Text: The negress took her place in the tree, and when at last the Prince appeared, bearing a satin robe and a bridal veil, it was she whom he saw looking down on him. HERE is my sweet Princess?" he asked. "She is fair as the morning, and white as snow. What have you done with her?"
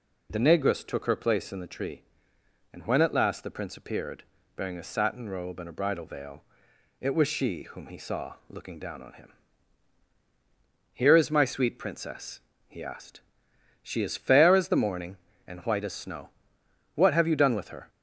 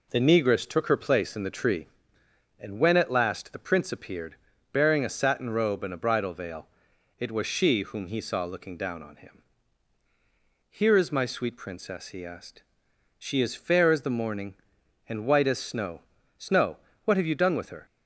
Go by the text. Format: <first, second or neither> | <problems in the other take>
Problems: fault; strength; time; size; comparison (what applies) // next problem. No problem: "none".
first | says "snow" twice; at 16.3 s